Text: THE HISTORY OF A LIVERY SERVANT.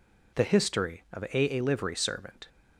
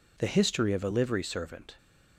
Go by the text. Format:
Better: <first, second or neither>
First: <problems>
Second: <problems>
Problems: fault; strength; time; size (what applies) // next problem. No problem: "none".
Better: second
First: says "A" twice; at 1.5 s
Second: none